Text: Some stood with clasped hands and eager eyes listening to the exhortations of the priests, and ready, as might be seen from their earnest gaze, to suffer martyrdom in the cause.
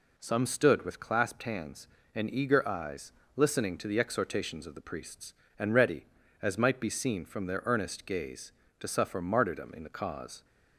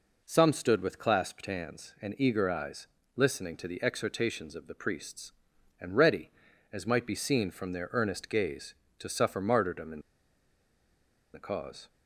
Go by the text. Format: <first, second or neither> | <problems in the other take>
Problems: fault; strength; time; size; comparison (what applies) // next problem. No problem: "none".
first | pauses between "eyes" and "listening"; slight; at 2.8 s; 0.28 s long; slight in the first // pauses between "in" and "the"; strong; at 9.9 s; 1.3 s long